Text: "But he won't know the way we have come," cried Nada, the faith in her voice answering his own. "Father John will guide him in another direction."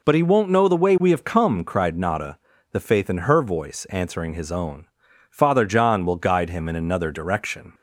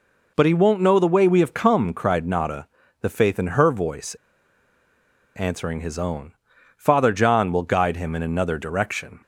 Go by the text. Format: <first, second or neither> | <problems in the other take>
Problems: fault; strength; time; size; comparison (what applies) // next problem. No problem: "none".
first | pauses between "voice" and "answering"; at 4.1 s; 1.2 s long